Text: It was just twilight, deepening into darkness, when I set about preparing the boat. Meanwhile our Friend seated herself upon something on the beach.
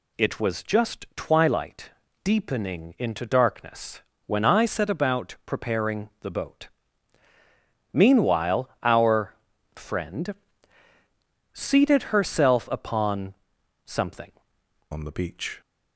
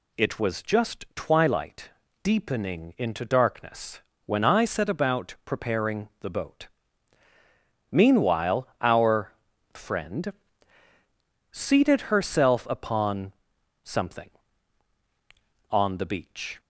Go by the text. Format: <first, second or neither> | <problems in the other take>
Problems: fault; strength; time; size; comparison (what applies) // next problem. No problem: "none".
second | pauses between "our" and "Friend"; at 9.3 s; 0.40 s long; also in the second // pauses between "Friend" and "seated"; at 10.3 s; 1.1 s long; also in the second // pauses between "upon" and "something"; noticeable; at 13.3 s; 0.52 s long; noticeable in the second // changes voice at "on"; from 14.9 s on; 0.7 s long